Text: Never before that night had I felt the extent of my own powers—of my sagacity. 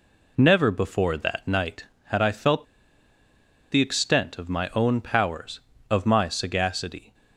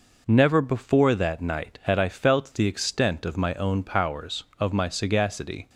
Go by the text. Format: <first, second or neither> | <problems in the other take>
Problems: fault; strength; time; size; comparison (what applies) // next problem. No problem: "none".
second | pauses between "felt" and "the"; at 2.6 s; 1.0 s long